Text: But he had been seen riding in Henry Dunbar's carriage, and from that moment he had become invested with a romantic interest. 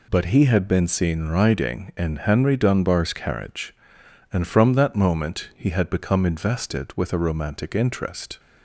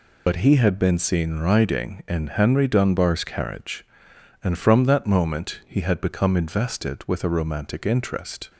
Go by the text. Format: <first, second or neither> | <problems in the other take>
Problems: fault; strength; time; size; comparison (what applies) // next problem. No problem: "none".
first | loses the start of "But"; at 0.2 s; 65 ms